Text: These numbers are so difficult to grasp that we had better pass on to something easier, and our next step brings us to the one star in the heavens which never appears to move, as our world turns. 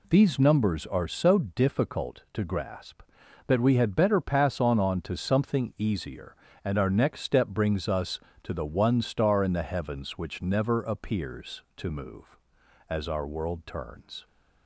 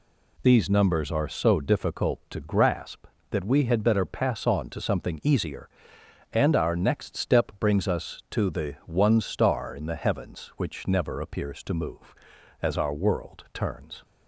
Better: second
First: says "on" twice; at 4.7 s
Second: none

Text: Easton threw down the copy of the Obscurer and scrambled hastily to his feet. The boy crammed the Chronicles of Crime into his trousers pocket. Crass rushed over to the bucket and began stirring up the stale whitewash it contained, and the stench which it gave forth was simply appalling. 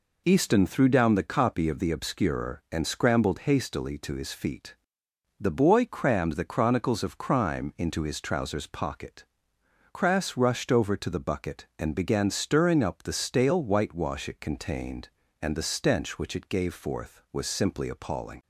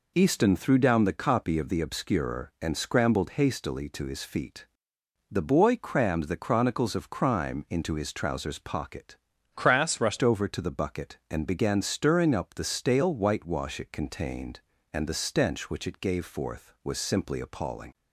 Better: first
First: none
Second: changes voice from "Crass" to "rushed"; from 9.5 to 10.2 s; 0.7 s long

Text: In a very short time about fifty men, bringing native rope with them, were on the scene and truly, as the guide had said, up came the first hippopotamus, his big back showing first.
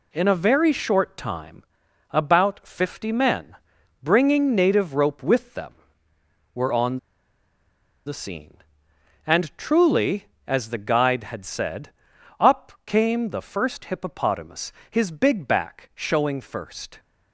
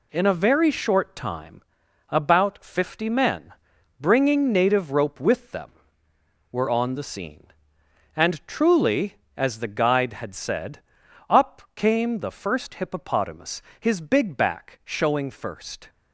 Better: second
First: pauses between "time" and "about"; noticeable; at 1.6 s; 0.48 s long // pauses between "on" and "the"; at 6.9 s; 1.0 s long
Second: pauses between "time" and "about"; noticeable; at 1.6 s; 0.48 s long

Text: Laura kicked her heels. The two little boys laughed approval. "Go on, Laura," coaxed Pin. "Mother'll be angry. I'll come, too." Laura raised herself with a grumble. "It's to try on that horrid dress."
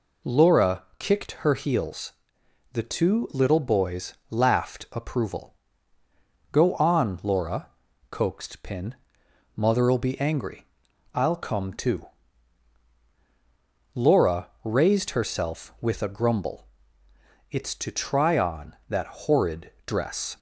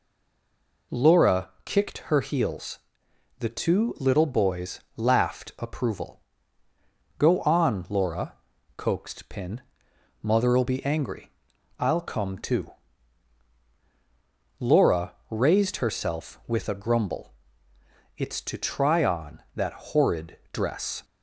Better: first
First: pauses between "boys" and "laughed"; slight; at 4.1 s; 0.16 s long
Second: stays silent before the first word; slight; until 0.9 s; 0.9 s long // pauses between "boys" and "laughed"; slight; at 4.7 s; 0.16 s long // pauses between "Laura" and "raised"; slight; at 15.1 s; 0.16 s long

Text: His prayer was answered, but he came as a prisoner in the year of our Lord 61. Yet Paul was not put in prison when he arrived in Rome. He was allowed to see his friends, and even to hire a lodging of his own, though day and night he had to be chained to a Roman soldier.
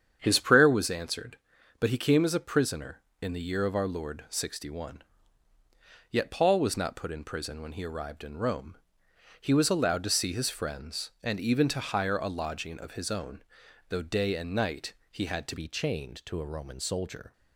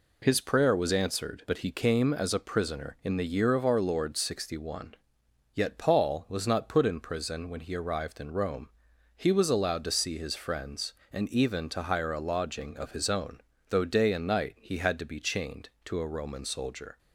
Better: second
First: starts louder than the rest; strong; until 1.2 s; 8 dB // pauses between "night" and "he"; slight; at 14.9 s; 0.18 s long // changes voice at "be"; from 15.5 s on; 1.8 s long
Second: none

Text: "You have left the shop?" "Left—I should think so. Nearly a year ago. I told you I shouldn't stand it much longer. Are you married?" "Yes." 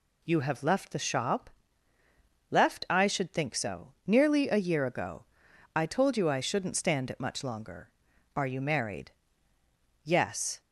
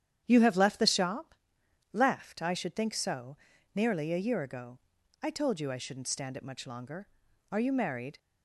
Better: first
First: none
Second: starts louder than the rest; strong; until 1.2 s; 9.5 dB // stops before "Yes"; at 8.1 s

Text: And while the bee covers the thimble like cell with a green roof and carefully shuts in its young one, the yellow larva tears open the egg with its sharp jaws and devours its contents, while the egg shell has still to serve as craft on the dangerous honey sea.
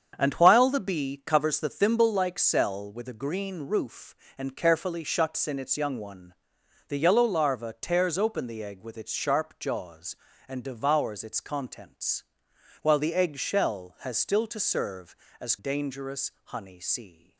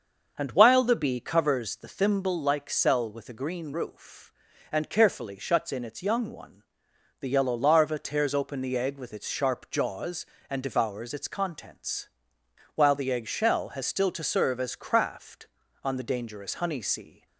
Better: second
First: starts louder than the rest; strong; until 1.1 s; 7.5 dB // skips "craft on the"; at 15.5 s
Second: starts louder than the rest; until 1.3 s; 6.5 dB

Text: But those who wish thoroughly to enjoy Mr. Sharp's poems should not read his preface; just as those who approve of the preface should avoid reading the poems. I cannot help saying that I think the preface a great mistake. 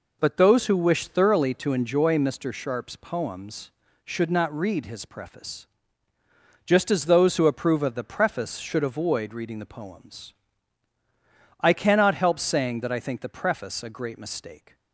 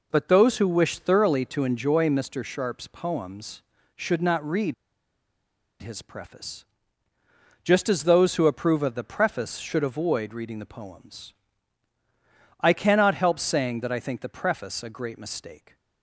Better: first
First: none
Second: pauses between "read" and "his"; at 4.7 s; 1.0 s long

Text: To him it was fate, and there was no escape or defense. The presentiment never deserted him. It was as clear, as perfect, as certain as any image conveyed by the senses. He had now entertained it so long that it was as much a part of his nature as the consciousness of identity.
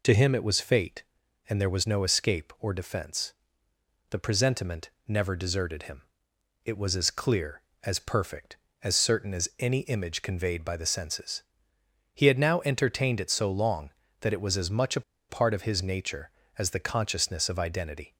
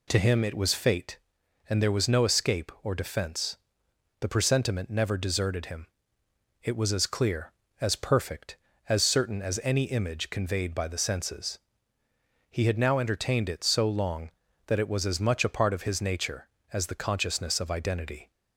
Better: second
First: pauses between "presentiment" and "never"; slight; at 4.8 s; 0.18 s long // pauses between "a" and "part"; slight; at 15.0 s; 0.28 s long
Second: none

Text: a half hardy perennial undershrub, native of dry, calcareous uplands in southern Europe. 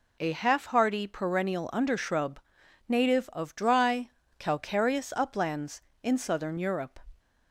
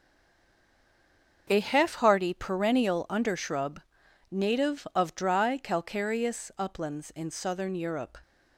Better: first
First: none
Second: stays silent before the first word; noticeable; until 1.4 s; 1.4 s long // starts louder than the rest; until 2.5 s; 6.5 dB

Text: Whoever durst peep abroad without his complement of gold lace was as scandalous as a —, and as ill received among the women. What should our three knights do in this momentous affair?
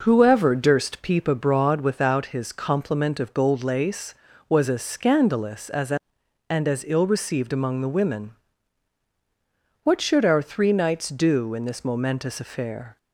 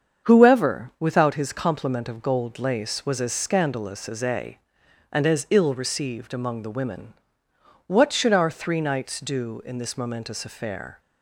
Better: first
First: none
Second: starts louder than the rest; strong; until 1.3 s; 7.5 dB // skips "durst peep abroad"; at 0.9 s

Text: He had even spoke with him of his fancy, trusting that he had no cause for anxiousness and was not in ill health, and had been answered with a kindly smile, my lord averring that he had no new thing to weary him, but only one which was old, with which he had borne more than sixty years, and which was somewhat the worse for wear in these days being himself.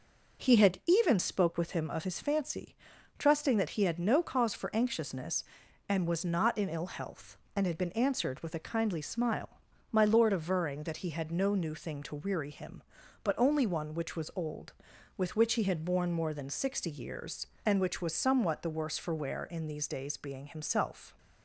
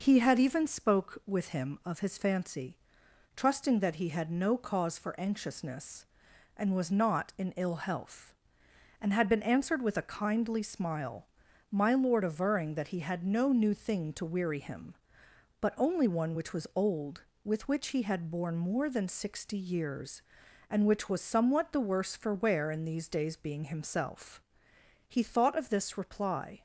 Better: first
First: none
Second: goes on to say "He thought of this reply"; from 25.0 s on; 1.5 s long

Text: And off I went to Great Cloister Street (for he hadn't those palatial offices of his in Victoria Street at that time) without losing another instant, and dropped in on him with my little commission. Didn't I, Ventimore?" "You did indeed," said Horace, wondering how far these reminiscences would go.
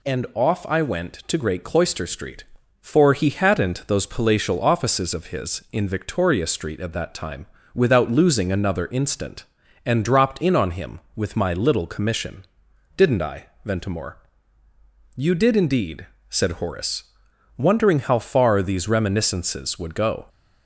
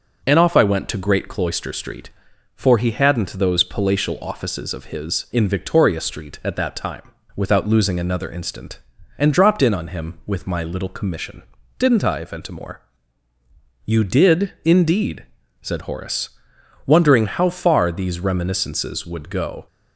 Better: neither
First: none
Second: none

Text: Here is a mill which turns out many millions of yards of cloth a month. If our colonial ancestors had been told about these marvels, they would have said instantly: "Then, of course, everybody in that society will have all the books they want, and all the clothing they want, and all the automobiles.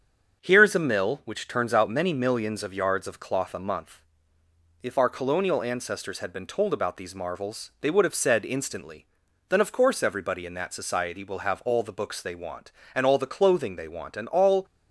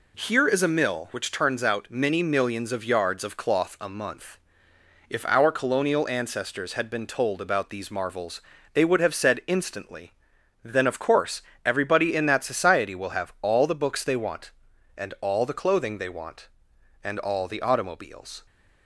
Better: second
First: starts louder than the rest; until 1.4 s; 7 dB // stops before "the automobiles"; at 14.6 s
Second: none

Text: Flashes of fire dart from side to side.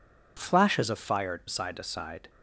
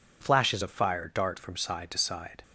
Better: second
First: skips "dart from"; at 1.4 s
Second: none

